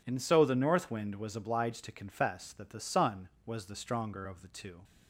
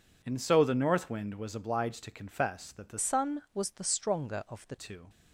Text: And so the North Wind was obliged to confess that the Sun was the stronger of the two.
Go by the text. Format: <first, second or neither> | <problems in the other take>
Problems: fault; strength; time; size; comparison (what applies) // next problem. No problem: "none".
first | changes voice from "Sun" to "the"; from 2.9 to 4.7 s; 1.8 s long